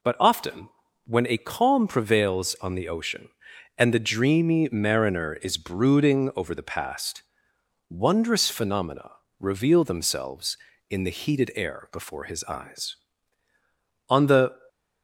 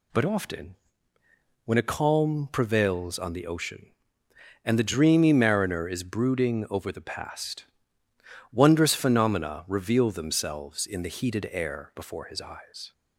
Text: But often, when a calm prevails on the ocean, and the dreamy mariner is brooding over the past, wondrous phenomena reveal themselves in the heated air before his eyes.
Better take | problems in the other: second | pauses between "phenomena" and "reveal"; slight; at 9.1 s; 0.28 s long // goes on to say "On the"; from 14.0 s on; 0.52 s long

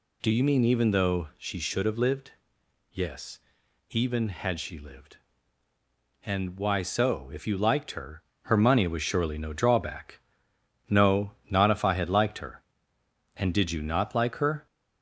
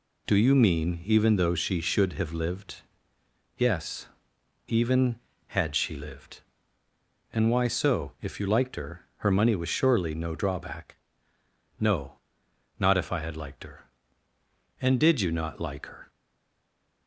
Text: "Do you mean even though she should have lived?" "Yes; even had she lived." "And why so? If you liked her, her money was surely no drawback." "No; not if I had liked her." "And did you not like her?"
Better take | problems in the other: first | stays silent after the last word; from 16.0 s on; 1.0 s long

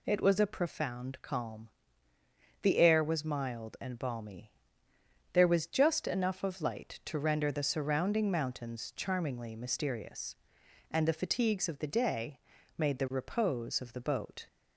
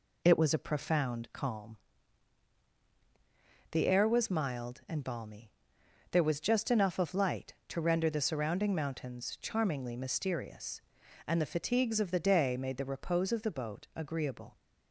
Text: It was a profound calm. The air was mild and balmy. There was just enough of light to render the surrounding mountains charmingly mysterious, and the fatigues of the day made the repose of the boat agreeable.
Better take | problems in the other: second | pauses between "day" and "made"; at 12.3 s; 0.38 s long // stops before "agreeable"; at 14.4 s

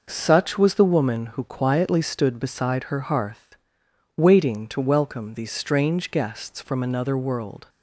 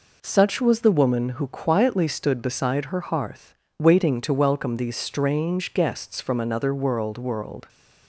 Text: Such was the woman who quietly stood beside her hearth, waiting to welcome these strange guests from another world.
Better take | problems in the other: first | says "world" twice; at 7.1 s

